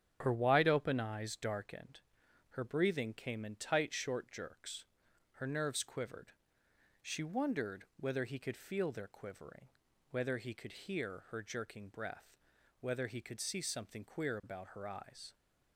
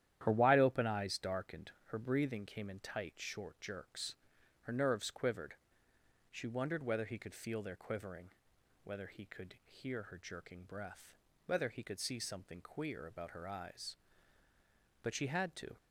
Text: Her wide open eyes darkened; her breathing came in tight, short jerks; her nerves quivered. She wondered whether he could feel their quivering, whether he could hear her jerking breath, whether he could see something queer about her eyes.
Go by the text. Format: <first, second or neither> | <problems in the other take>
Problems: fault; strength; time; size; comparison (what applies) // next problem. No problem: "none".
first | starts louder than the rest; strong; until 1.2 s; 11 dB; strong in the first // goes on to say "But she had to"; noticeable; from 15.0 s on; 0.74 s long